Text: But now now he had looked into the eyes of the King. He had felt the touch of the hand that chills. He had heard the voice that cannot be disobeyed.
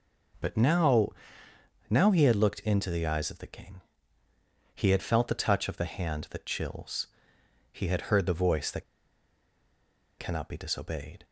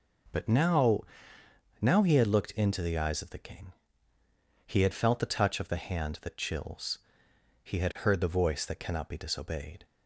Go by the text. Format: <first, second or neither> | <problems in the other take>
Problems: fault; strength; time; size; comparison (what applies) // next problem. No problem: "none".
second | pauses between "now" and "now"; noticeable; at 1.0 s; 0.80 s long; noticeable in the second // pauses between "that" and "cannot"; strong; at 8.8 s; 1.3 s long